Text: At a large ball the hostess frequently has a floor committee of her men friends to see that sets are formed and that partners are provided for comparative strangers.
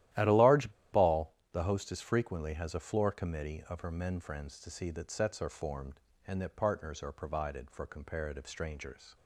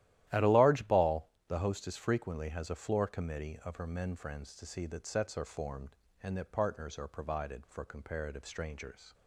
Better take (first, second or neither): second